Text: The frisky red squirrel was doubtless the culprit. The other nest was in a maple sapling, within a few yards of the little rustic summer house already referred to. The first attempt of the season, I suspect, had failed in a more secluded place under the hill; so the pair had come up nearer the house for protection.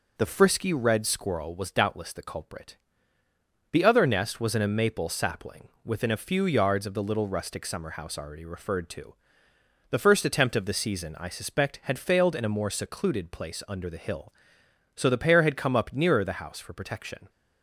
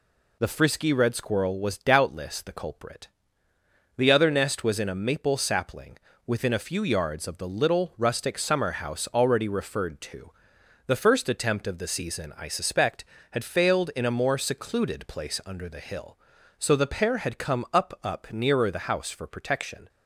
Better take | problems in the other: first | says "up" twice; at 18.0 s

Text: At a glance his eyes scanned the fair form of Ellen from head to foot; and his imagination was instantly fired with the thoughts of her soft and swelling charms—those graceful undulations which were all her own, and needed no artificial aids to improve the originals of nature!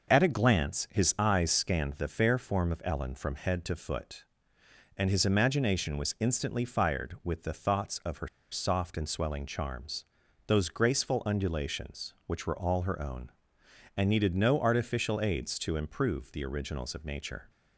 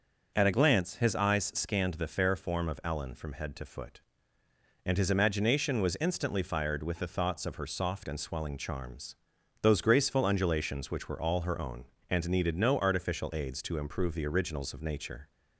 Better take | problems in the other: second | pauses between "her" and "soft"; slight; at 8.2 s; 0.24 s long

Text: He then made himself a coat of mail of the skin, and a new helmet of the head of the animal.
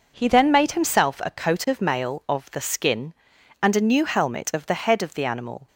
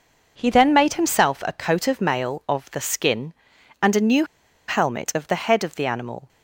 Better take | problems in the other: first | pauses between "new" and "helmet"; at 4.2 s; 0.43 s long

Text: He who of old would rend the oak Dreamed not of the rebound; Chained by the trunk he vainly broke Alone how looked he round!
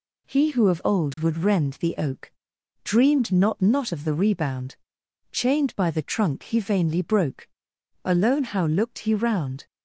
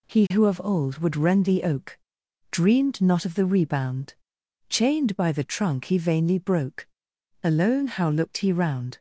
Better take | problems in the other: second | pauses between "oak" and "Dreamed"; noticeable; at 2.3 s; 0.52 s long; noticeable in the second // says "not" twice; at 3.5 s // pauses between "broke" and "Alone"; noticeable; at 7.4 s; 0.56 s long; noticeable in the second

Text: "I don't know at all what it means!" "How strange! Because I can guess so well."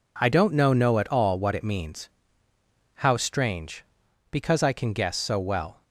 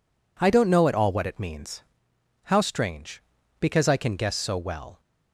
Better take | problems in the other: second | says "know" twice; at 0.7 s

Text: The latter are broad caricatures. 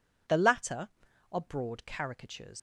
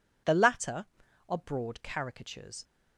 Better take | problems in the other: second | leaves "caricatures" unfinished; at 2.5 s; 65 ms

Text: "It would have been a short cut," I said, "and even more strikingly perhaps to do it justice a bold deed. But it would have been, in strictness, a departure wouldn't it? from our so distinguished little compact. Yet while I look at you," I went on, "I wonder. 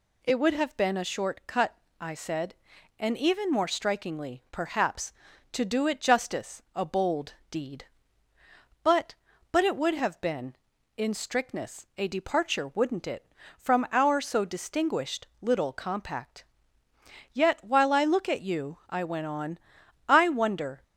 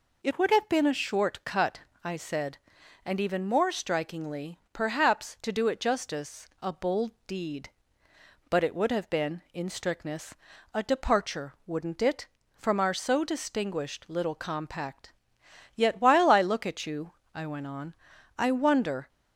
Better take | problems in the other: second | pauses between "bold" and "deed"; slight; at 7.3 s; 0.16 s long; slight in the second // says "But" twice; at 9.5 s

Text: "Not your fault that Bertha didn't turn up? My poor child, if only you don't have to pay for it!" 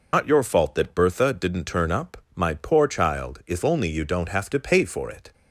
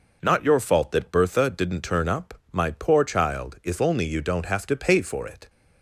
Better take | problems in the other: second | loses the start of "Not"; at 0.1 s; 85 ms

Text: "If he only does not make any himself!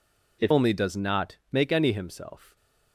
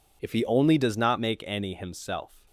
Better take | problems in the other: second | skips "he"; at 0.5 s // pauses between "not" and "make"; slight; at 1.3 s; 0.16 s long

